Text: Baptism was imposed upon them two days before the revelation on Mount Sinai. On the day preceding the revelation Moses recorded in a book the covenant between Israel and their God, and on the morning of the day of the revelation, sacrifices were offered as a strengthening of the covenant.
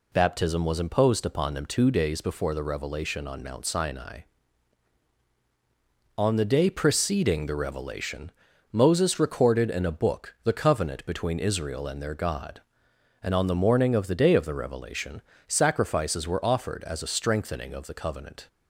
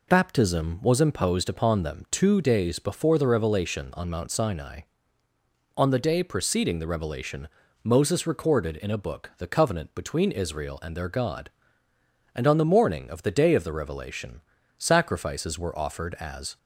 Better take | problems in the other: first | pauses between "revelation" and "Moses"; slight; at 7.4 s; 0.36 s long; also in the first // stops before "a strengthening of the covenant"; at 16.5 s

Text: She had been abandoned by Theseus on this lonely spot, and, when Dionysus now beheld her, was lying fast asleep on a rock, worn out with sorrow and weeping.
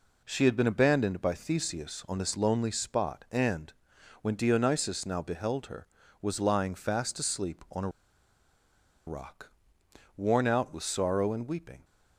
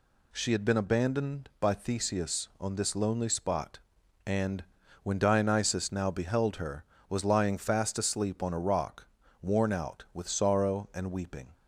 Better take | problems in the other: second | pauses between "a" and "rock"; at 7.8 s; 1.1 s long

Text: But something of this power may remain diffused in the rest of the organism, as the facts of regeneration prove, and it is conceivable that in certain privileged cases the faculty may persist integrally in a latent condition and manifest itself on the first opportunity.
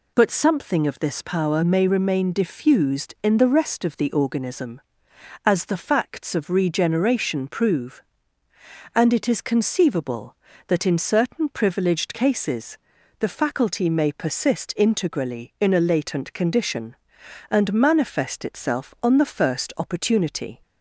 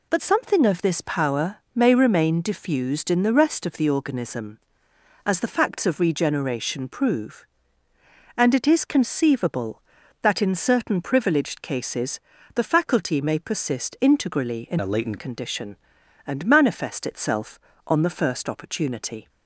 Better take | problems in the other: first | pauses between "power" and "may"; slight; at 1.5 s; 0.18 s long // pauses between "cases" and "the"; slight; at 12.1 s; 0.34 s long; also in the first // changes voice from "a" to "latent"; from 14.7 to 15.1 s; 0.4 s long

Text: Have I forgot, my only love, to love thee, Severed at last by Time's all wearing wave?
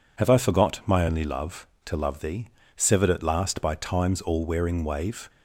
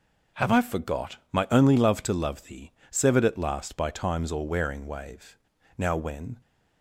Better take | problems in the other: first | goes on to say "Now when"; from 5.7 s on; 0.58 s long

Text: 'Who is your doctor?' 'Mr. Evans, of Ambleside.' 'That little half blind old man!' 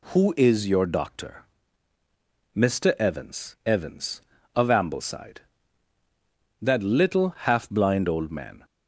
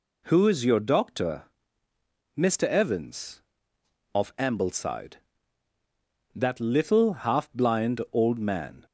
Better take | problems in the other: second | says "Evans" twice; at 3.6 s

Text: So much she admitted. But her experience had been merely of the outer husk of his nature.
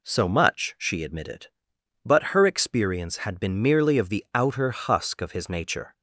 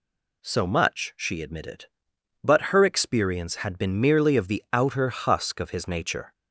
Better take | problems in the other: second | starts louder than the rest; slight; until 1.5 s; 3 dB

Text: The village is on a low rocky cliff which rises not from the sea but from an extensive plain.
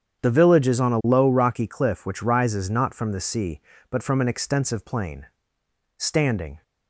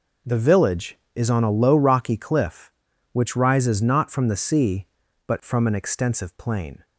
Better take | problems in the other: second | starts louder than the rest; strong; until 1.2 s; 8.5 dB // goes on to say "Standing"; noticeable; from 5.9 s on; 0.66 s long

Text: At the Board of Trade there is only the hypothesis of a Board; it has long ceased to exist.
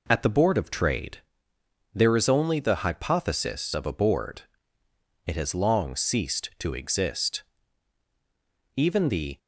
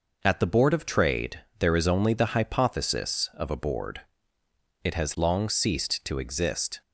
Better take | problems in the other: second | pauses between "Trade" and "there"; noticeable; at 1.1 s; 0.74 s long; slight in the second // goes on to say "Even the"; noticeable; from 8.7 s on; 0.62 s long

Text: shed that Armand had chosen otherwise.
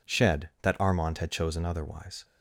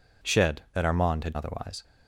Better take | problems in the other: first | skips "chosen"; at 1.3 s

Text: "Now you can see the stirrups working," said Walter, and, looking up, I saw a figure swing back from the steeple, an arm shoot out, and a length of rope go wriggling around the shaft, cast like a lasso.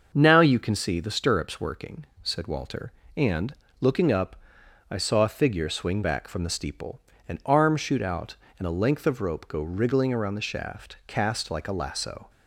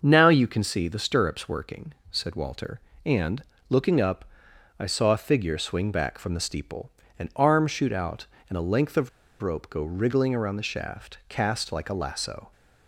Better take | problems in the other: first | starts louder than the rest; until 1.0 s; 6.5 dB; also in the first // pauses between "of" and "rope"; slight; at 9.0 s; 0.33 s long

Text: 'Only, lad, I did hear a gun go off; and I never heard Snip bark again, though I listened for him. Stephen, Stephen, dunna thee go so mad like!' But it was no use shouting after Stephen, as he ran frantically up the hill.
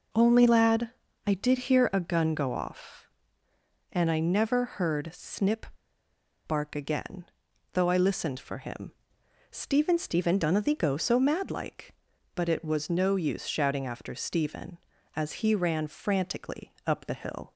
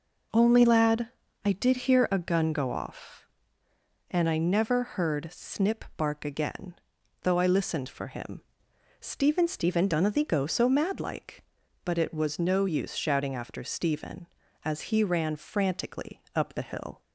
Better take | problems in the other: second | pauses between "Snip" and "bark"; noticeable; at 5.6 s; 0.82 s long

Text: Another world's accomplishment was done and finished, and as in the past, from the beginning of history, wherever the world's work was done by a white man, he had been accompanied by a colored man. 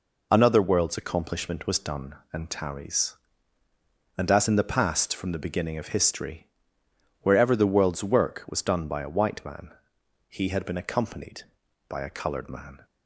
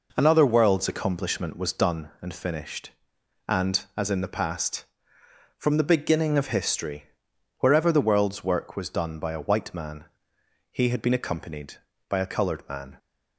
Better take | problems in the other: second | says "tarries" for "finished"; at 2.4 s

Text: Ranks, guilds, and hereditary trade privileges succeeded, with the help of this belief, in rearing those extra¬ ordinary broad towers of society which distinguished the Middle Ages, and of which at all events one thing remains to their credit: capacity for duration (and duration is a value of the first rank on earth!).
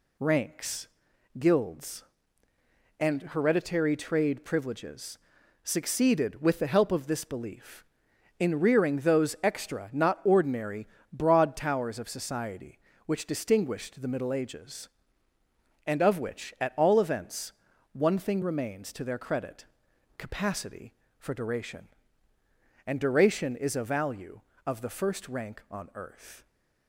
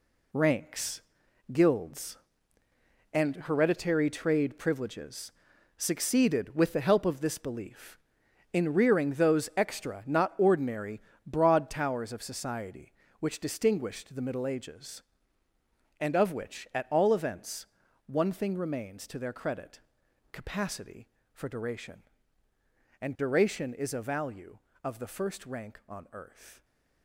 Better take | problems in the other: first | gets quieter; strong; throughout; 9.5 dB // pauses between "privileges" and "succeeded"; noticeable; at 5.2 s; 0.46 s long; noticeable in the first // pauses between "ordinary" and "broad"; slight; at 11.0 s; 0.24 s long; slight in the first // pauses between "events" and "one"; at 17.6 s; 0.40 s long; also in the first

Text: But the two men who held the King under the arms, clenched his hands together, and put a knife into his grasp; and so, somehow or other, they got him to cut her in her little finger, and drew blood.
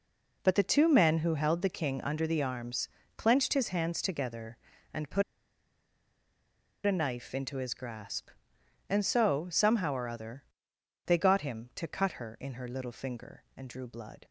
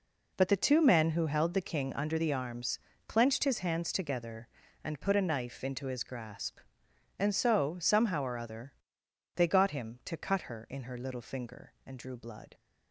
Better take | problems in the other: second | pauses between "put" and "a"; strong; at 5.2 s; 1.6 s long

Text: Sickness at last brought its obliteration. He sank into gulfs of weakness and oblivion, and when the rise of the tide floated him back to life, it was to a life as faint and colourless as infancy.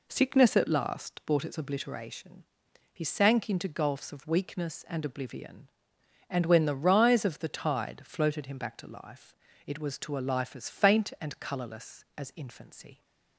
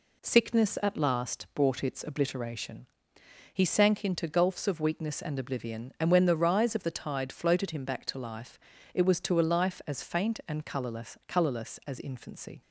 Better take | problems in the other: first | says "colourless" twice; at 11.2 s

